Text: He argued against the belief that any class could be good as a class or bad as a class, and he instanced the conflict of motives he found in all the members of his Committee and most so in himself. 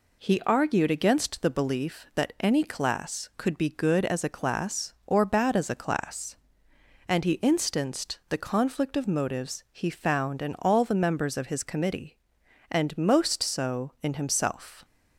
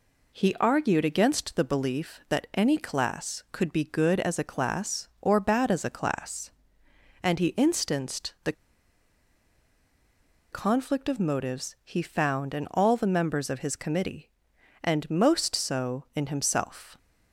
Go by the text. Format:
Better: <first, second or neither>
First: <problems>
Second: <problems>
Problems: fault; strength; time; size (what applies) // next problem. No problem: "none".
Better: first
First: none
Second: pauses between "the" and "conflict"; strong; at 8.5 s; 2.0 s long